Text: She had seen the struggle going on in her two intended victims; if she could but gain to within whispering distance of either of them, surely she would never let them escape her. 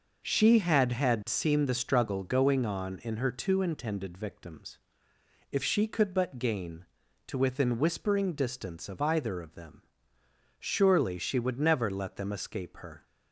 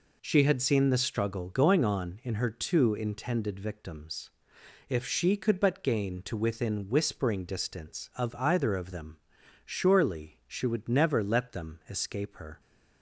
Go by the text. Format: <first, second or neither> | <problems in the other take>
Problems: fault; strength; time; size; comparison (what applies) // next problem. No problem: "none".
second | says "had" twice; at 0.9 s